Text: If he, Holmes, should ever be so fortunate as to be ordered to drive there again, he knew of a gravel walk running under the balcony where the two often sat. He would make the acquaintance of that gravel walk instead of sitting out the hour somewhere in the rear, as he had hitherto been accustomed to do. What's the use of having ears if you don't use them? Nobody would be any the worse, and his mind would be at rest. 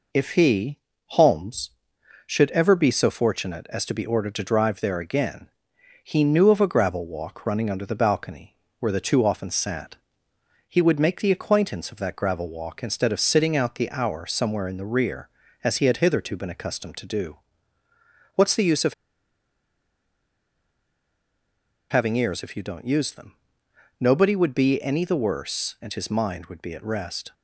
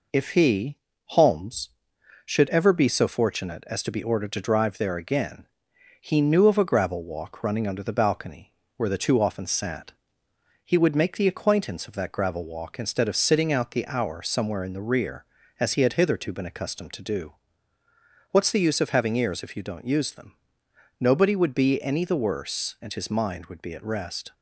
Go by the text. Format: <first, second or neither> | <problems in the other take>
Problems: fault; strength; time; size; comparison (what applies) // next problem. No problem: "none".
second | pauses between "balcony" and "where"; slight; at 8.5 s; 0.24 s long; slight in the second // pauses between "of" and "having"; strong; at 18.9 s; 2.9 s long